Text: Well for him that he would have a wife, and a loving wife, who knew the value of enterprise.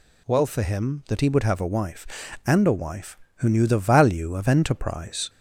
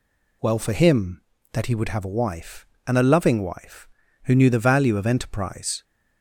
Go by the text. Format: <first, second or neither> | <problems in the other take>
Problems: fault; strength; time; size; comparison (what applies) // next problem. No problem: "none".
second | skips "loving"; at 2.7 s